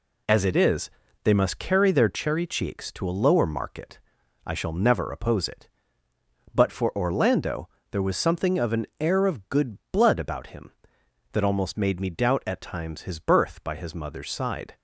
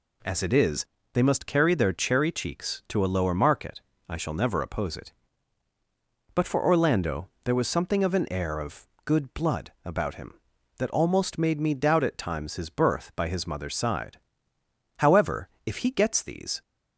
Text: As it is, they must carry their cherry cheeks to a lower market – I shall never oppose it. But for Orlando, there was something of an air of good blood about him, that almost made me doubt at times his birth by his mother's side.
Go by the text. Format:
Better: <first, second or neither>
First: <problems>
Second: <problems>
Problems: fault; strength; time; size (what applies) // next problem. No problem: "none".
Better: first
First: none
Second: pauses between "of" and "good"; slight; at 8.8 s; 0.18 s long // goes on to say "However if he gets these"; from 14.9 s on; 1.6 s long